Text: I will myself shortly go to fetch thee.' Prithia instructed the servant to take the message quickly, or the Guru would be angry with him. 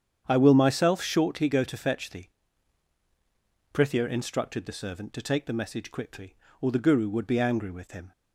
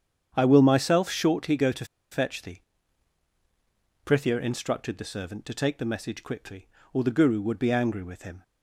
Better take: first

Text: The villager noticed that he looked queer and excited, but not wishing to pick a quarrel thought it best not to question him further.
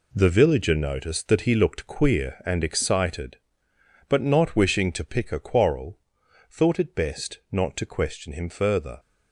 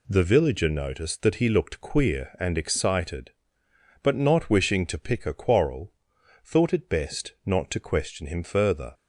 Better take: second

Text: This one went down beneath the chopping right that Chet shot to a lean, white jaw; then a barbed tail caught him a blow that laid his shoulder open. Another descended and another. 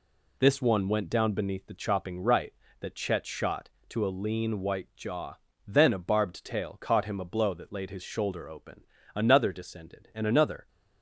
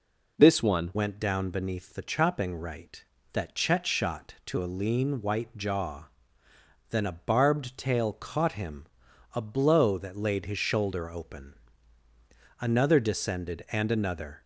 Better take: first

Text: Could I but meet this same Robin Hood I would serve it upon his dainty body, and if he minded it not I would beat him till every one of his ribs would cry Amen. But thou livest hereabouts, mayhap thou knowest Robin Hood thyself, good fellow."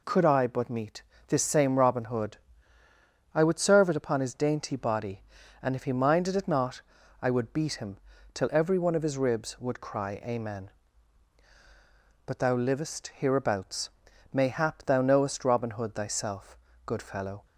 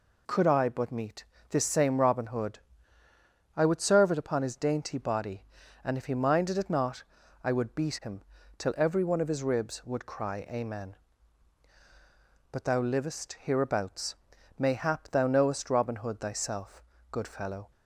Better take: neither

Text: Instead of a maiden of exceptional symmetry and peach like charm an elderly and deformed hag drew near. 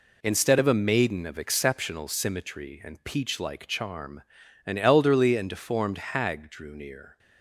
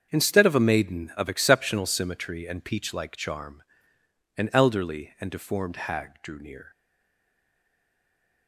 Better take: first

